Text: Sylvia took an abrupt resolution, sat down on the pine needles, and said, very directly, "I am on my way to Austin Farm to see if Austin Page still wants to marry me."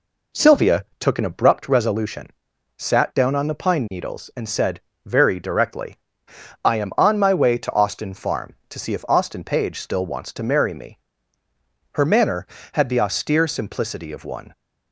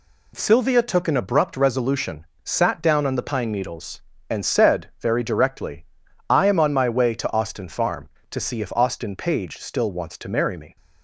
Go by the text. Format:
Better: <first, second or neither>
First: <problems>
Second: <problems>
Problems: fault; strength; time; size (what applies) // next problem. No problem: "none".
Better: second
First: goes on to say "Her manner had the austere simplicity of one"; strong; from 11.9 s on; 2.6 s long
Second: none